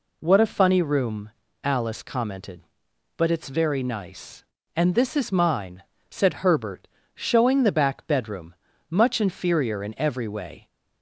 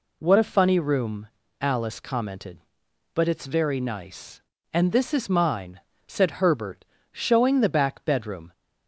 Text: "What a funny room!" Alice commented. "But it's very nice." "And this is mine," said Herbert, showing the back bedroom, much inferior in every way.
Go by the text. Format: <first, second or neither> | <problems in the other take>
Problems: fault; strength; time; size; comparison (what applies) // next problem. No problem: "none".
first | stops before "much inferior in every way"; at 8.5 s